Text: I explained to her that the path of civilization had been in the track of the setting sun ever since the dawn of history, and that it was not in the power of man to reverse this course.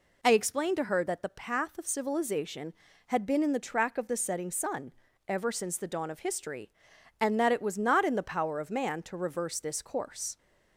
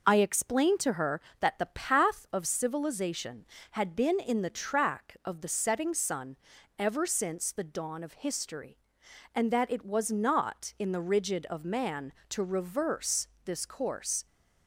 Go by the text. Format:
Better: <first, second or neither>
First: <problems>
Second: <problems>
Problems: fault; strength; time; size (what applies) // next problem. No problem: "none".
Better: first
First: pauses between "sun" and "ever"; slight; at 4.9 s; 0.36 s long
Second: pauses between "sun" and "ever"; at 6.3 s; 0.42 s long // says "rigid" for "power"; at 10.9 s // pauses between "reverse" and "this"; slight; at 13.2 s; 0.18 s long